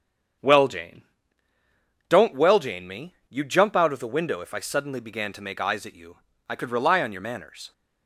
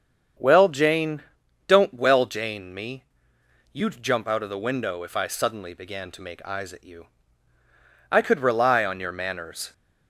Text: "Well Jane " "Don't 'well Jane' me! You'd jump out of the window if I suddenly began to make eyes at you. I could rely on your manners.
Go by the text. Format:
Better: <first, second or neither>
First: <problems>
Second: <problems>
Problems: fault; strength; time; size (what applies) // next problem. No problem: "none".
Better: neither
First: none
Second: none